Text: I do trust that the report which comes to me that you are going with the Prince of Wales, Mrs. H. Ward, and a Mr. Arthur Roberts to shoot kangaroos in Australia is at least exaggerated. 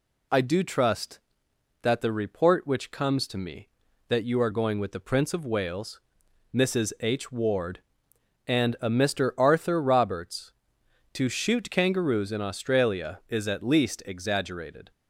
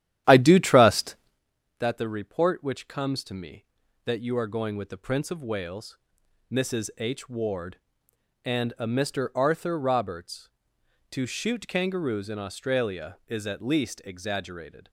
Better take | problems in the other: first | starts louder than the rest; strong; until 1.4 s; 12 dB

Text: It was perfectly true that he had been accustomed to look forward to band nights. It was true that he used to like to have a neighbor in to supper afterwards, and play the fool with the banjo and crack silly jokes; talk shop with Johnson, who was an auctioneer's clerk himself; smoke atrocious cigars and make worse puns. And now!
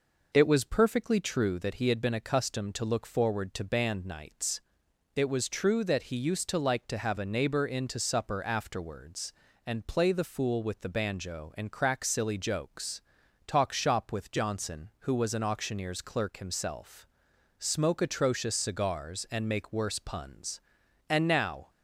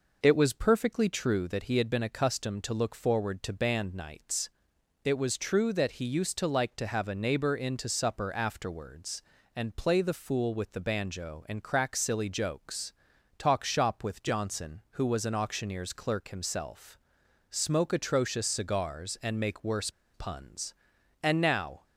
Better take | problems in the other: first | pauses between "worse" and "puns"; slight; at 19.8 s; 0.24 s long

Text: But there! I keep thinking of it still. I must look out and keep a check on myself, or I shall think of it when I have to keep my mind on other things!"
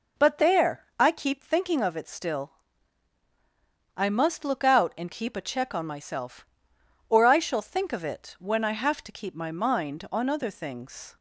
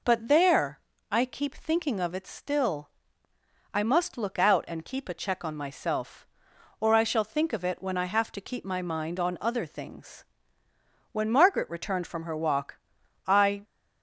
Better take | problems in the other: first | goes on to say "When Margaret returned from her walk I"; strong; from 11.1 s on; 2.5 s long

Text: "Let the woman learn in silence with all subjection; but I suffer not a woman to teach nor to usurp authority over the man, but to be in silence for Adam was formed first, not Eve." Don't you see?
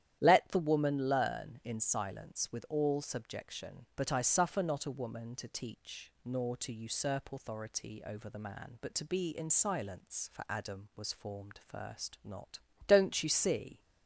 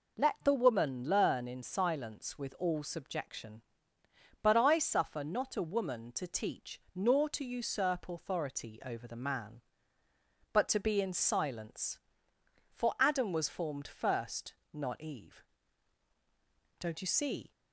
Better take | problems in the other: second | starts louder than the rest; strong; until 1.2 s; 10.5 dB // skips "Eve"; at 12.7 s

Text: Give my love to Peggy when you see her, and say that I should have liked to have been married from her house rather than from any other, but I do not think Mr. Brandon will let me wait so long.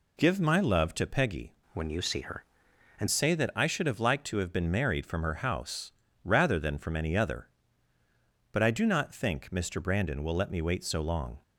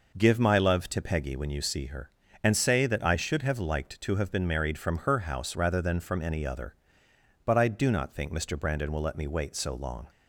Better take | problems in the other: second | changes voice from "when" to "and"; from 1.7 to 3.0 s; 1.3 s long // pauses between "house" and "rather"; slight; at 5.9 s; 0.32 s long

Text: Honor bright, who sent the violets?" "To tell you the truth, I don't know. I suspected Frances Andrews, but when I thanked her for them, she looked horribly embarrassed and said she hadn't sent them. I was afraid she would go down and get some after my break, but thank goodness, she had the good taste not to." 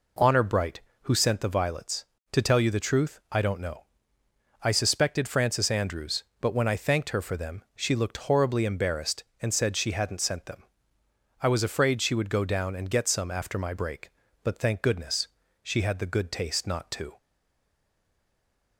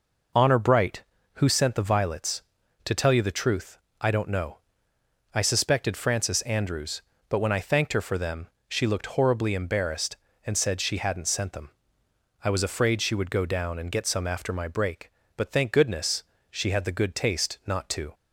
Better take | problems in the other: second | stays silent after the last word; noticeable; from 17.1 s on; 1.6 s long

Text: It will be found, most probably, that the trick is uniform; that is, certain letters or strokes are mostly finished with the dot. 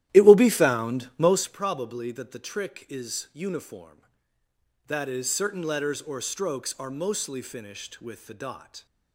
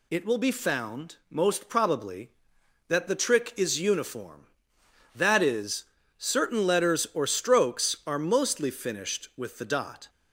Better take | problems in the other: second | starts louder than the rest; strong; until 1.6 s; 13 dB

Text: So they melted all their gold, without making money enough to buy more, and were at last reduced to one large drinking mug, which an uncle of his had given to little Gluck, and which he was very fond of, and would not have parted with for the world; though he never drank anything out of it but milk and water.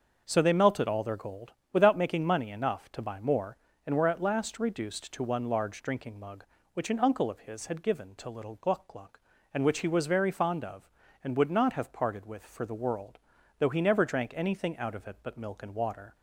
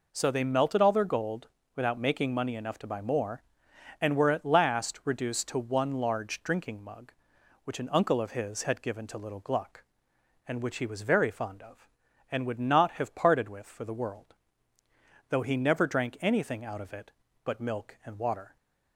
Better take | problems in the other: second | starts louder than the rest; until 1.2 s; 6.5 dB // says "Gluck" twice; at 8.8 s

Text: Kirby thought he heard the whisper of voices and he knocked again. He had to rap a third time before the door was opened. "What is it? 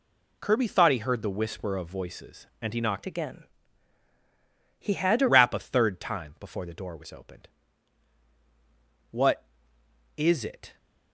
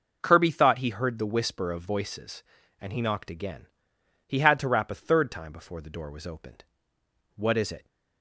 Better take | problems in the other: second | changes voice from "again" to "to"; from 3.0 to 5.2 s; 2.2 s long

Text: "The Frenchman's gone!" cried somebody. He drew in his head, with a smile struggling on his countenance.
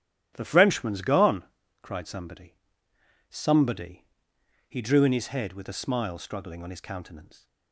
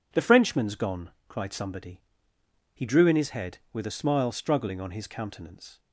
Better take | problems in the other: second | starts louder than the rest; strong; until 1.3 s; 13 dB // says "somebody" twice; at 3.3 s

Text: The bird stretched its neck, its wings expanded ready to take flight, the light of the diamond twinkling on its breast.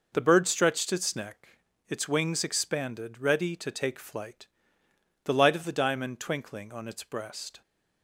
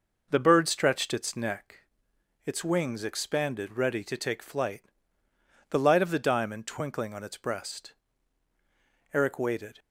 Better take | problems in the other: first | goes on to say "Eric waited"; noticeable; from 9.1 s on; 0.66 s long

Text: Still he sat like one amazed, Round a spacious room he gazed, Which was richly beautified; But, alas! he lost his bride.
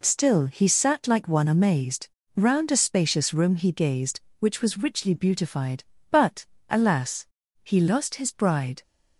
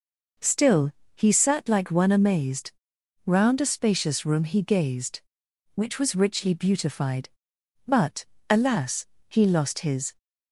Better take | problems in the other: first | pauses between "Still" and "he"; slight; at 0.9 s; 0.24 s long // stops before "bride"; at 10.1 s

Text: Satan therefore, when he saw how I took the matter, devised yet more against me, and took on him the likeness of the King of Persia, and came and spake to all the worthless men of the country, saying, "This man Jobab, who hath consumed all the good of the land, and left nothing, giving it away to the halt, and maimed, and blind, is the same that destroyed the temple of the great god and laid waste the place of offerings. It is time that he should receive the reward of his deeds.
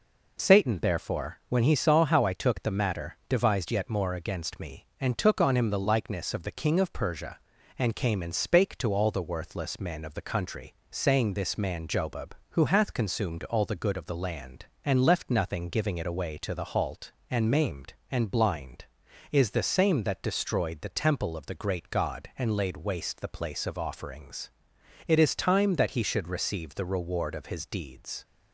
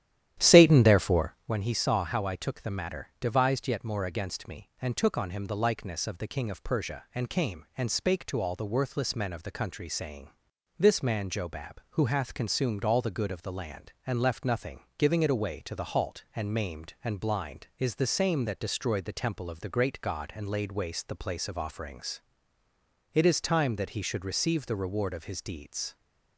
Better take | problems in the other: first | starts louder than the rest; strong; until 1.4 s; 11.5 dB

